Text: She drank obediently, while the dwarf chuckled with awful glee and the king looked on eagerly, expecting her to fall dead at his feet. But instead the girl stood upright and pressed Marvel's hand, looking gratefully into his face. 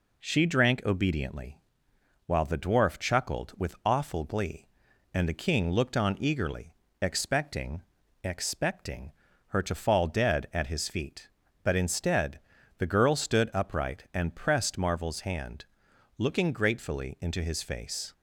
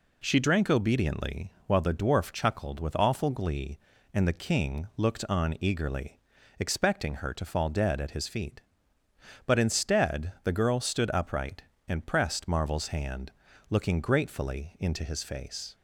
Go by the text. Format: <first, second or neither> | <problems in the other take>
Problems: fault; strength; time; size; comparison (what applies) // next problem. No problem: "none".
second | says "expecting" twice; at 8.2 s // pauses between "instead" and "the"; at 12.3 s; 0.38 s long